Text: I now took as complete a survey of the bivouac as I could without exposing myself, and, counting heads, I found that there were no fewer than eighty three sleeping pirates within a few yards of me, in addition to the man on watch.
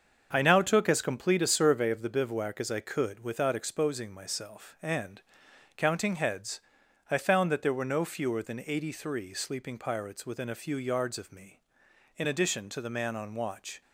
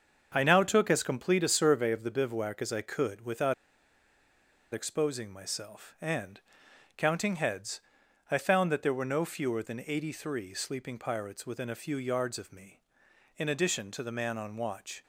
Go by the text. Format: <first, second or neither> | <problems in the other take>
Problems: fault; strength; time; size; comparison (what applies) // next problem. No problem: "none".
first | starts louder than the rest; until 1.3 s; 6.5 dB; also in the first // pauses between "without" and "exposing"; at 3.5 s; 1.2 s long